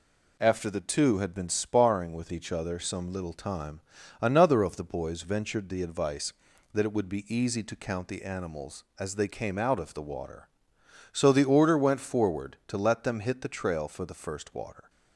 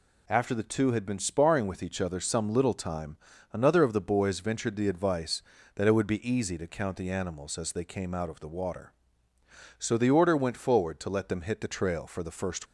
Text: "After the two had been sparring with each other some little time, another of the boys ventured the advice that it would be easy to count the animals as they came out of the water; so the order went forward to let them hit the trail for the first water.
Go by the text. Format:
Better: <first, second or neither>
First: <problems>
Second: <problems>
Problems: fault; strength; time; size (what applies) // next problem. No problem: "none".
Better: first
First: none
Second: stops before "water"; at 12.6 s